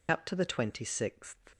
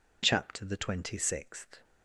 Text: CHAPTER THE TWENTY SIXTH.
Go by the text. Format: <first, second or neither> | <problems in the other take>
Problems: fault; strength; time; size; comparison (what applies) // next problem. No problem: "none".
second | loses the start of "CHAPTER"; at 0.0 s; 105 ms